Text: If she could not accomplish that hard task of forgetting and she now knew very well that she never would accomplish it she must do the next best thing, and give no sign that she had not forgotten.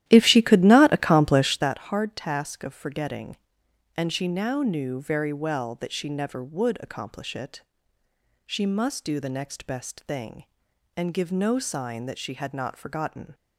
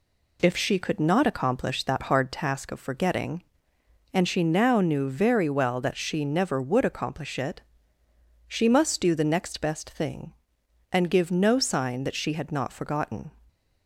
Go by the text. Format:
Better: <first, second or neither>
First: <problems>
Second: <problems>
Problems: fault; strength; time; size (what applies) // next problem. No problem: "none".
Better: second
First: starts louder than the rest; strong; until 1.7 s; 13 dB // pauses between "it" and "she"; noticeable; at 7.6 s; 0.84 s long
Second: pauses between "it" and "she"; noticeable; at 7.6 s; 0.88 s long